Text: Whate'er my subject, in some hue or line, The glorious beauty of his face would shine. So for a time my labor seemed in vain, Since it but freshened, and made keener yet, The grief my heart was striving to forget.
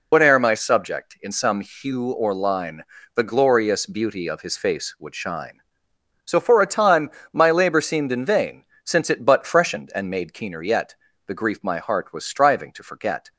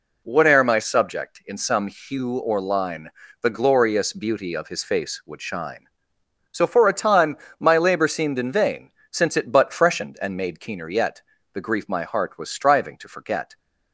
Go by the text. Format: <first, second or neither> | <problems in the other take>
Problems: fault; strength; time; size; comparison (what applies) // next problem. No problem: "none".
second | loses the start of "Whate'er"; at 0.1 s; 125 ms // pauses between "time" and "my"; slight; at 7.0 s; 0.22 s long; slight in the second